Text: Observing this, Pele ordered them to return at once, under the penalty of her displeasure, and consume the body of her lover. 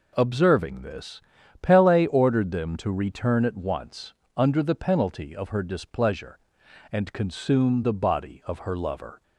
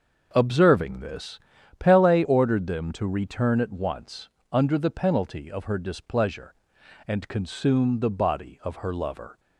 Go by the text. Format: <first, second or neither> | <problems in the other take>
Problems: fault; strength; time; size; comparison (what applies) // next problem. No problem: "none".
first | starts louder than the rest; until 1.7 s; 6.5 dB